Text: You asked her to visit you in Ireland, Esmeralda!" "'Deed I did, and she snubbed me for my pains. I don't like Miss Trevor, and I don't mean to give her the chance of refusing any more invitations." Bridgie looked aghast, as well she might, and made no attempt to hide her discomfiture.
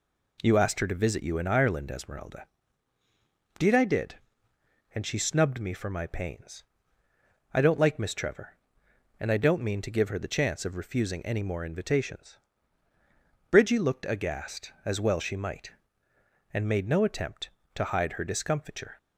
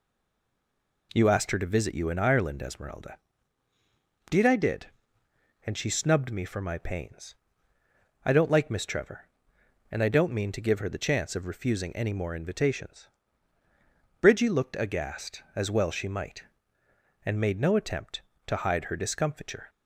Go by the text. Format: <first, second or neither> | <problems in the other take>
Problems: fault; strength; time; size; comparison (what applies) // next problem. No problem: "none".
first | stays silent before the first word; until 1.1 s; 1.1 s long